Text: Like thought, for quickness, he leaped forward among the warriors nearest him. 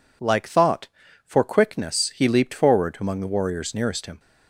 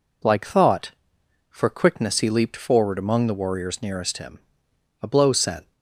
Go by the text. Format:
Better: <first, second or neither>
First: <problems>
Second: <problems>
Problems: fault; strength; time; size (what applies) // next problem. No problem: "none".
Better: first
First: none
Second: goes on to say "A blow sent"; noticeable; from 5.0 s on; 0.70 s long